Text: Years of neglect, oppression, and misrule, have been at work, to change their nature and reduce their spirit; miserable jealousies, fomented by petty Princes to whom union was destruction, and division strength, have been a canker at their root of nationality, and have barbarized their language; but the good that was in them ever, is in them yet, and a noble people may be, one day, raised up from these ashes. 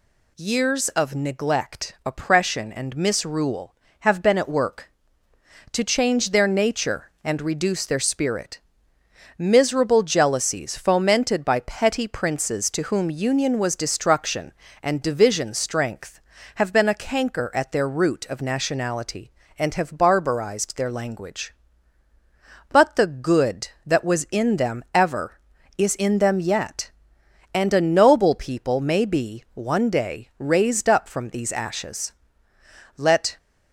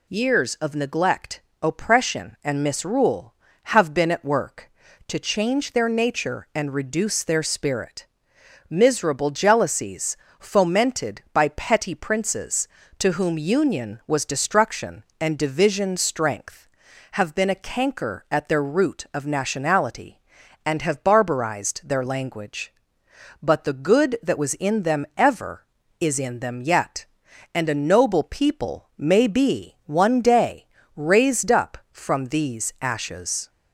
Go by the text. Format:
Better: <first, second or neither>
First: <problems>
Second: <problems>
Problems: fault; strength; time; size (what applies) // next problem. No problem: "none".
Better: second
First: goes on to say "Let"; slight; from 32.9 s on; 0.40 s long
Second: none